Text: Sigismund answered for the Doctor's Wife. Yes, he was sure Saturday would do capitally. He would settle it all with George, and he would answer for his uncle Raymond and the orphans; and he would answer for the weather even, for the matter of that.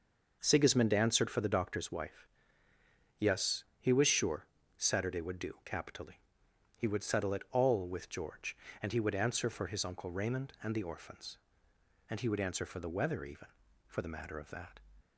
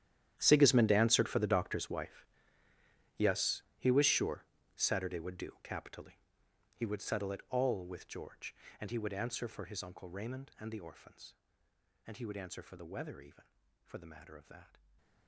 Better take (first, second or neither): first